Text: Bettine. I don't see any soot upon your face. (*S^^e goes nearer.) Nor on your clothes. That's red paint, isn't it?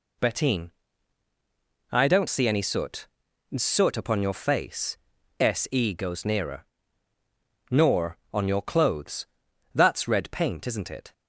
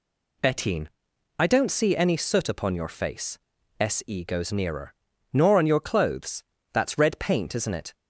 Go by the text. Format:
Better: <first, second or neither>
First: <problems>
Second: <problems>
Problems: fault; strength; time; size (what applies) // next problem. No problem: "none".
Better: second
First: says "soot" twice; at 3.5 s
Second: none